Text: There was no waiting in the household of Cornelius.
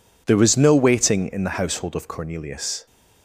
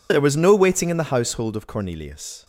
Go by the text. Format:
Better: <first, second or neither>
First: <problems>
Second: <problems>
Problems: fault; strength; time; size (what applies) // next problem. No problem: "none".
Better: neither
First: none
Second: none